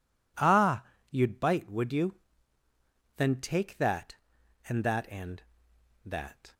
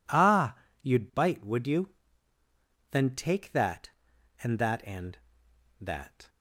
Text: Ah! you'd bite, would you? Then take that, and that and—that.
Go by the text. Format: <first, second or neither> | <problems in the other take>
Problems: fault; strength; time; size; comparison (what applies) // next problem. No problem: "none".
neither | none